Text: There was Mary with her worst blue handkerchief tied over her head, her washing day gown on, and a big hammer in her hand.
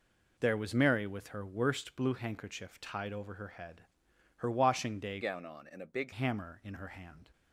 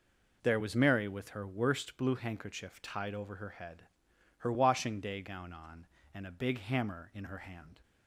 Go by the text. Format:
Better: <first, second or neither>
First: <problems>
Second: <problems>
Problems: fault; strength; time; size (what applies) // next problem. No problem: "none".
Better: second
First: changes voice from "gown" to "big"; from 5.2 to 6.1 s; 0.9 s long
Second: none